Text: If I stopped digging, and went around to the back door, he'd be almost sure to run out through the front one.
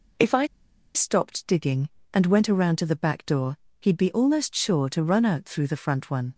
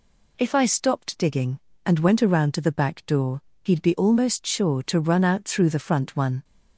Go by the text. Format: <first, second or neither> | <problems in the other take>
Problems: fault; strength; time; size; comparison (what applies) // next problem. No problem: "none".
second | pauses between "I" and "stopped"; noticeable; at 0.4 s; 0.48 s long